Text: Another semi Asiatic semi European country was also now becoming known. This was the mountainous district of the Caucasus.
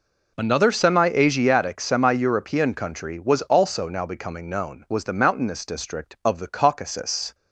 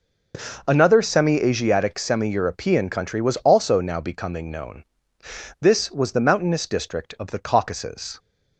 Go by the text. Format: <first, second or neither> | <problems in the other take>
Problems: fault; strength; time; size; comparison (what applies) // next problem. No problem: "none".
second | skips "This"; at 4.8 s